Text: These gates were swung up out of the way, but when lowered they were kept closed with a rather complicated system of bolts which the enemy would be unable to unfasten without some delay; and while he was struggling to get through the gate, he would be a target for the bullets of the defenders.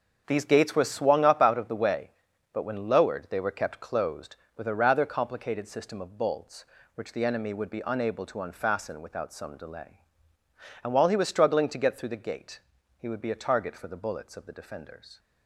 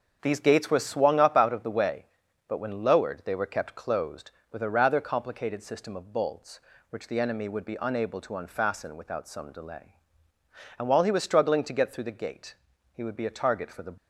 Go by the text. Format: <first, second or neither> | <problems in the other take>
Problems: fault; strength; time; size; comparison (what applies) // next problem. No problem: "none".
first | starts louder than the rest; until 1.2 s; 6.5 dB; also in the first // stops before "bullets of the defenders"; at 13.9 s